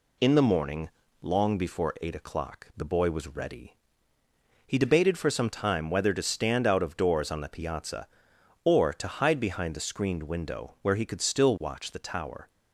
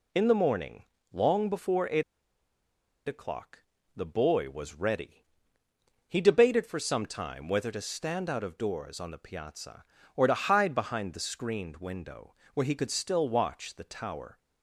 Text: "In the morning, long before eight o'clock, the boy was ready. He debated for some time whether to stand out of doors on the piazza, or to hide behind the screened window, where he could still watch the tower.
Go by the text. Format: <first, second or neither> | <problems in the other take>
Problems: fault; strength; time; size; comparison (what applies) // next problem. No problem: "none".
first | pauses between "eight" and "o'clock"; at 2.0 s; 1.0 s long